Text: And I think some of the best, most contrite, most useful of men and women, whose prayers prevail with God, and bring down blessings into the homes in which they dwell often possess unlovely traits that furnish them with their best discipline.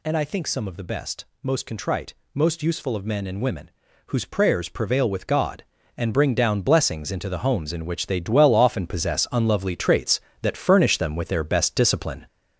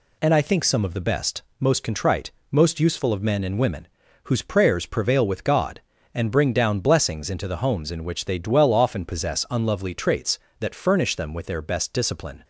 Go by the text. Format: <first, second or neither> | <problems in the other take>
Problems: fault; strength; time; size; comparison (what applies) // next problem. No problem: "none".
second | gets louder; noticeable; throughout; 5 dB